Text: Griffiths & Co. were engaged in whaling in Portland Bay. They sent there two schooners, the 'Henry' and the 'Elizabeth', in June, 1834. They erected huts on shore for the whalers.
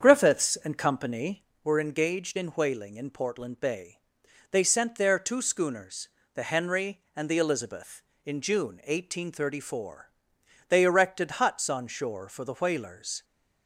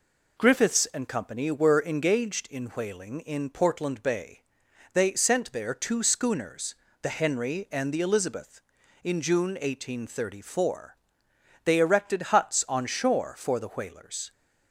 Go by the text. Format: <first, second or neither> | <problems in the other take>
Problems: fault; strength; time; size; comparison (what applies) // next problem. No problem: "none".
second | starts louder than the rest; strong; until 1.6 s; 7.5 dB